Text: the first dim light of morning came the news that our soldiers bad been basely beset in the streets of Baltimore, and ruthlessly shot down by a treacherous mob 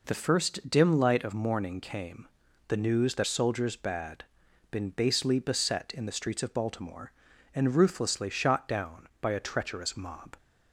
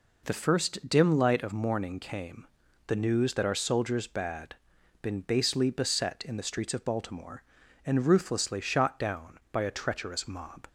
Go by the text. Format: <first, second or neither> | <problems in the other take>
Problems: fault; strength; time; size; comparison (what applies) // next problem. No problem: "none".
second | pauses between "came" and "the"; at 2.2 s; 0.40 s long; also in the second // skips "our"; at 3.2 s // pauses between "bad" and "been"; noticeable; at 4.2 s; 0.48 s long; noticeable in the second